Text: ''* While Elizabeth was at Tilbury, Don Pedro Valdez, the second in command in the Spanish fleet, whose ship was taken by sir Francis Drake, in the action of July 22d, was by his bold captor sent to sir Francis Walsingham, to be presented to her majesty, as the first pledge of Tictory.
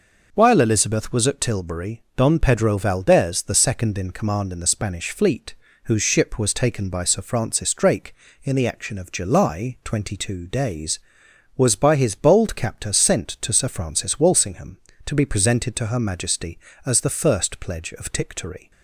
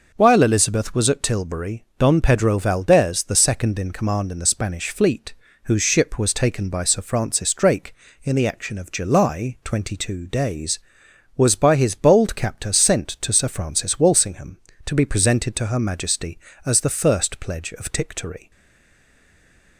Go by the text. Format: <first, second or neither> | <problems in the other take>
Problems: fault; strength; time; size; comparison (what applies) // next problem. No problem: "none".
first | stays silent after the last word; noticeable; from 18.5 s on; 1.2 s long